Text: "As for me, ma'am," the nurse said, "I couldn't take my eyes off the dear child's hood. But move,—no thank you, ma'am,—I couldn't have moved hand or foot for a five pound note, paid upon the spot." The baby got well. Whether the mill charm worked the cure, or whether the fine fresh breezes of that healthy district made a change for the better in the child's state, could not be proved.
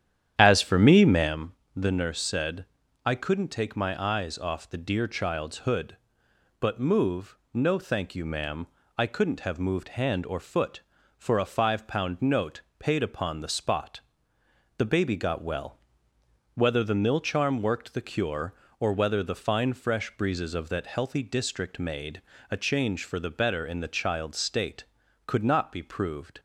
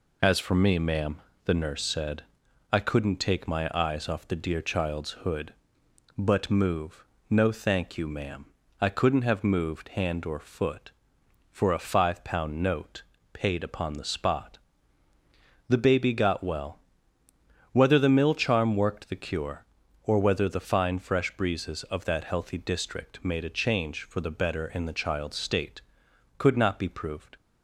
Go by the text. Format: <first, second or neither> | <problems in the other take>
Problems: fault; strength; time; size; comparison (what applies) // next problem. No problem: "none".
second | starts louder than the rest; strong; until 1.4 s; 10 dB // pauses between "made" and "a"; slight; at 22.2 s; 0.28 s long